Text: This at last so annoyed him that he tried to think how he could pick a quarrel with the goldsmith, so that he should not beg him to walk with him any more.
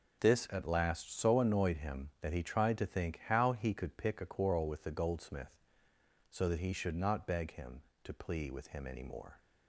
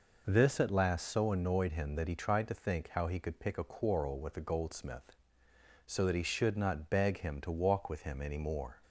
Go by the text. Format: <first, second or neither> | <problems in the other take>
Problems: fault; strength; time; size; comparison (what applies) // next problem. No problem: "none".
second | says "plea" for "walk"; at 8.1 s